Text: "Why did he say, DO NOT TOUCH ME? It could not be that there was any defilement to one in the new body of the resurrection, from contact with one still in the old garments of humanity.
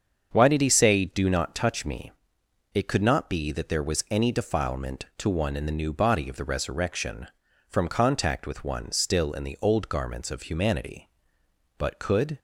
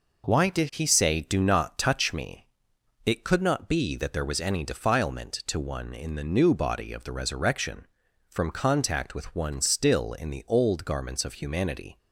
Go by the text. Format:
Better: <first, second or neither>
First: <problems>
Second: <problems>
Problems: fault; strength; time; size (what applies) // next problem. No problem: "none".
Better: second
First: starts louder than the rest; until 1.3 s; 7 dB // goes on to say "But could"; from 11.7 s on; 0.60 s long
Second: none